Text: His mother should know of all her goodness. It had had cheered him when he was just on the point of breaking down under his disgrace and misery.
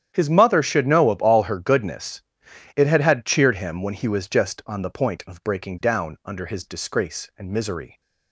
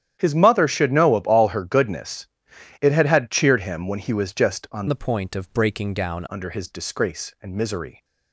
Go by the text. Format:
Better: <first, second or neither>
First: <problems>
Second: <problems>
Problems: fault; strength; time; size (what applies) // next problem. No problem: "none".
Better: first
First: starts louder than the rest; strong; until 1.1 s; 9.5 dB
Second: starts louder than the rest; strong; until 1.2 s; 10 dB // changes voice from "the" to "down"; from 4.8 to 6.2 s; 1.4 s long